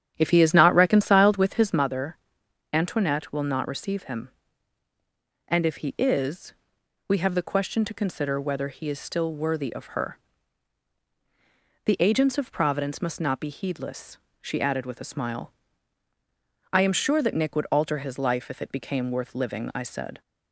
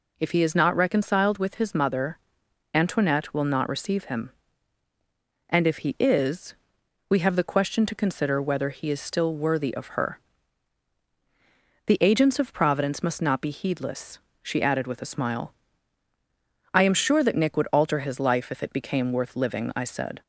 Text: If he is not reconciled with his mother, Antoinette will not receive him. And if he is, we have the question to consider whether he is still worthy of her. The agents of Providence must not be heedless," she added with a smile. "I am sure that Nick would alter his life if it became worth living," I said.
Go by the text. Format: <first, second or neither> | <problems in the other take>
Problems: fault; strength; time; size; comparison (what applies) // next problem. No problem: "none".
second | starts louder than the rest; strong; until 1.9 s; 9.5 dB